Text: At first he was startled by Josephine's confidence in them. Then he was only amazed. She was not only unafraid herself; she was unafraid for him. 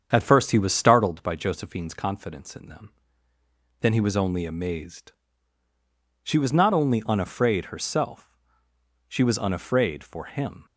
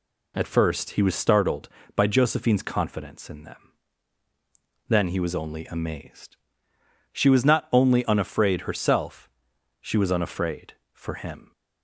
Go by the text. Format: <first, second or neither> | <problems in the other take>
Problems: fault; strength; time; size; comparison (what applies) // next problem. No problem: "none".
second | starts louder than the rest; strong; until 1.2 s; 7.5 dB